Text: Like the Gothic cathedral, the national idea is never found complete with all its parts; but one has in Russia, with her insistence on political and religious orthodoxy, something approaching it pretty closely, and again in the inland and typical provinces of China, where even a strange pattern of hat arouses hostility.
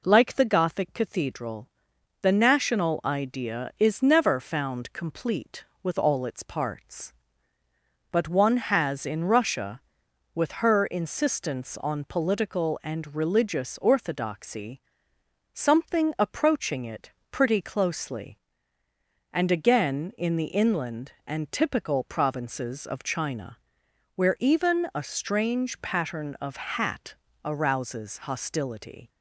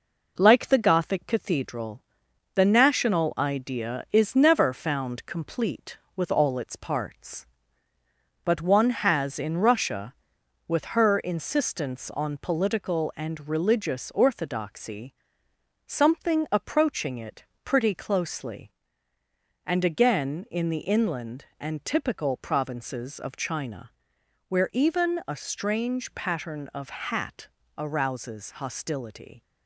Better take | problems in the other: first | gets quieter; throughout; 4 dB // pauses between "it" and "pretty"; slight; at 17.4 s; 0.18 s long; slight in the first // pauses between "hat" and "arouses"; slight; at 27.4 s; 0.30 s long; slight in the first

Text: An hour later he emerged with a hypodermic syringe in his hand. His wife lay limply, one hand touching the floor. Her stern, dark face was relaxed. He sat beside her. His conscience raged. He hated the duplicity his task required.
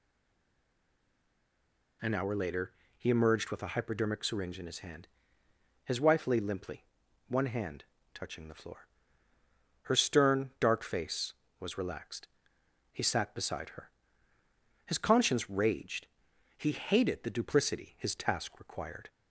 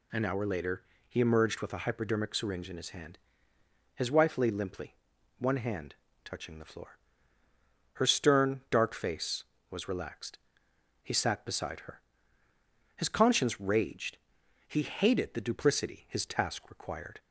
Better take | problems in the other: second | stays silent before the first word; noticeable; until 2.0 s; 2.0 s long // pauses between "later" and "he"; slight; at 2.7 s; 0.24 s long; slight in the second // pauses between "hand" and "touching"; slight; at 7.8 s; 0.30 s long; slight in the second

